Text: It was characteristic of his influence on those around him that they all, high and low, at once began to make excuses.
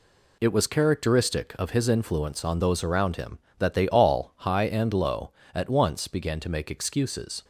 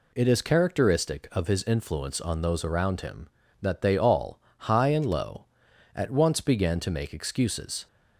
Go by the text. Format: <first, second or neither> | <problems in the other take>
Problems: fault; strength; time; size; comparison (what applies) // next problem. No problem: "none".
first | says "is" for "was"; at 0.2 s